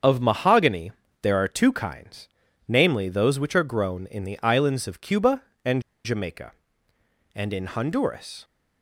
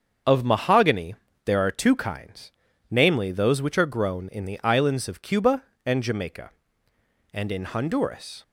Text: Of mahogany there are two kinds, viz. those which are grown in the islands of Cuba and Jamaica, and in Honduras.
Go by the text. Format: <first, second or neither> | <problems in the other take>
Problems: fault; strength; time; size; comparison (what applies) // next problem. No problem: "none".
second | starts louder than the rest; until 1.3 s; 7 dB; also in the second // pauses between "mahogany" and "there"; slight; at 0.9 s; 0.30 s long; slight in the second // pauses between "and" and "Jamaica"; slight; at 5.8 s; 0.23 s long